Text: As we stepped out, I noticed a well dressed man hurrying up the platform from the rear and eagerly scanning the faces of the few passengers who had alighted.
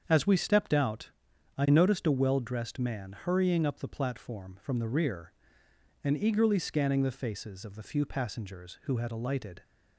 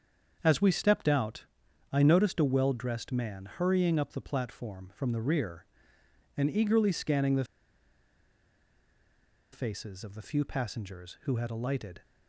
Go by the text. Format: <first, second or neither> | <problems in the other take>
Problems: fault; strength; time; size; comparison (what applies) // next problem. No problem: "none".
first | starts louder than the rest; strong; until 1.4 s; 7 dB; strong in the first // pauses between "the" and "faces"; strong; at 7.4 s; 2.0 s long